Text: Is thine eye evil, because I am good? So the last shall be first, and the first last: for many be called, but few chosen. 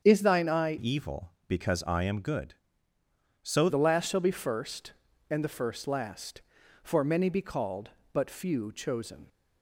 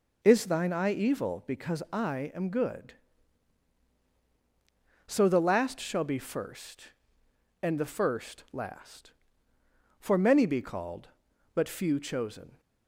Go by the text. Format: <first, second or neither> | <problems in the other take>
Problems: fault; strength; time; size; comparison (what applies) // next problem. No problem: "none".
second | starts louder than the rest; strong; until 1.0 s; 7.5 dB // changes voice from "evil" to "So"; from 0.7 to 3.6 s; 2.9 s long